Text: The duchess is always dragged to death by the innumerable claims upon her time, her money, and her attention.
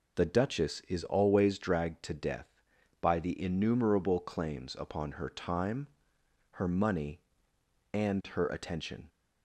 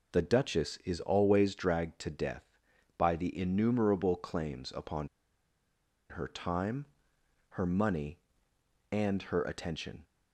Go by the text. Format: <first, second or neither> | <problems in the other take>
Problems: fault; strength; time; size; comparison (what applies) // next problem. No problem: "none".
first | pauses between "upon" and "her"; at 5.0 s; 1.0 s long